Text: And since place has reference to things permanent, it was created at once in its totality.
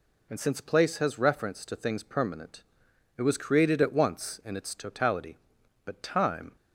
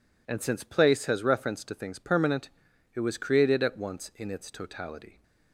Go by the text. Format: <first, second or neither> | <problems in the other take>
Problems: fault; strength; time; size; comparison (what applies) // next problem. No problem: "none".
second | goes on to say "But time"; noticeable; from 5.8 s on; 0.70 s long